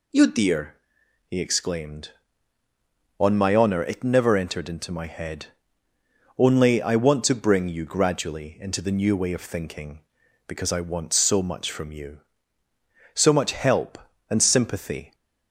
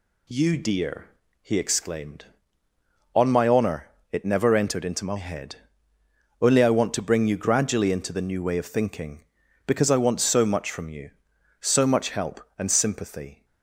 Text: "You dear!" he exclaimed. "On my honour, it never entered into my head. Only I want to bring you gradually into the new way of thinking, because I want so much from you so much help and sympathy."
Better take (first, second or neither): neither